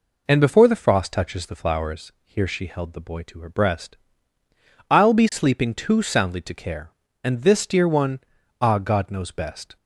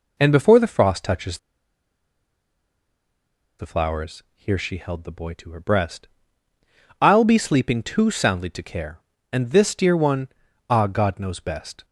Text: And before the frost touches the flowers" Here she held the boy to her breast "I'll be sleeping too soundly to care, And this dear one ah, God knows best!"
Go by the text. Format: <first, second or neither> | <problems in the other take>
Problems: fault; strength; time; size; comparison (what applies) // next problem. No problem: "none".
first | pauses between "touches" and "the"; strong; at 1.3 s; 2.2 s long // pauses between "breast" and "I'll"; noticeable; at 6.0 s; 0.94 s long; noticeable in the first // pauses between "one" and "ah"; at 10.2 s; 0.40 s long; also in the first